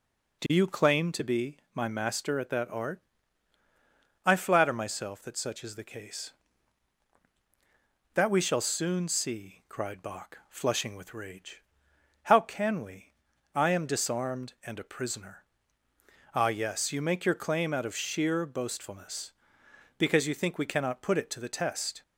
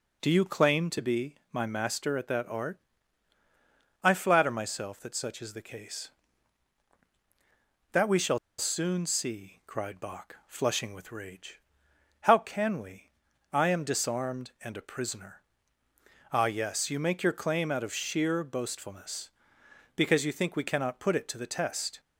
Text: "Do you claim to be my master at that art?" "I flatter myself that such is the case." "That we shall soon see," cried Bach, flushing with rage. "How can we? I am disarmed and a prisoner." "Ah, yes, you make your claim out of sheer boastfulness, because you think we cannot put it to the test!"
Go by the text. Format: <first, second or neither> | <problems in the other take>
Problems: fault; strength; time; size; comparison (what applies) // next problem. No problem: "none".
first | pauses between "shall" and "soon"; slight; at 8.3 s; 0.20 s long